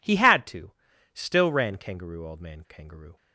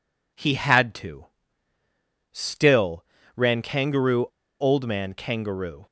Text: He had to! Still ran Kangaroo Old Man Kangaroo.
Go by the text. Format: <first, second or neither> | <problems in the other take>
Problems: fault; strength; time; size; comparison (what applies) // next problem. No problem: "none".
first | pauses between "Still" and "ran"; slight; at 3.0 s; 0.32 s long // pauses between "Kangaroo" and "Old"; slight; at 4.2 s; 0.33 s long